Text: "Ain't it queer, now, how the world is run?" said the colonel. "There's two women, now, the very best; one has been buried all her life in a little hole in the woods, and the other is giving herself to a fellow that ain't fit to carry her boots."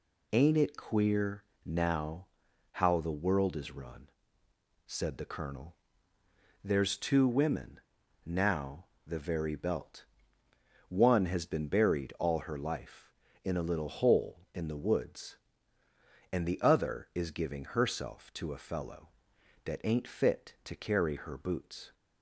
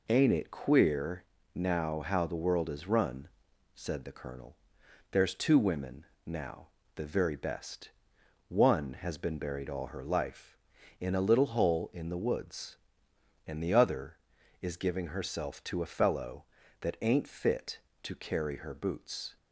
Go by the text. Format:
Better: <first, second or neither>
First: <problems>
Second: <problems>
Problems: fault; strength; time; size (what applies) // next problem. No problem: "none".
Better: second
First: says "belt" for "best"; at 9.5 s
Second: none